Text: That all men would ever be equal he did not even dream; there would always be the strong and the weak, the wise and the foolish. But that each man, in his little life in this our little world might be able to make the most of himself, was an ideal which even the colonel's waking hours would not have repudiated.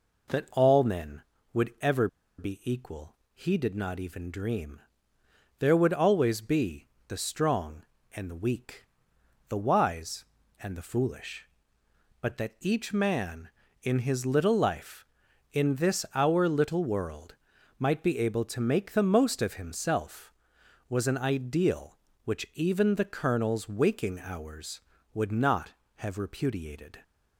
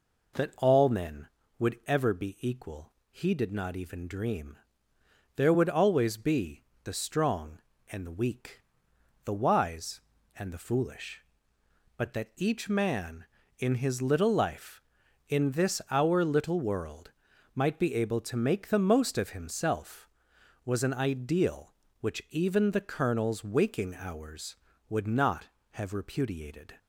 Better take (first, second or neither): second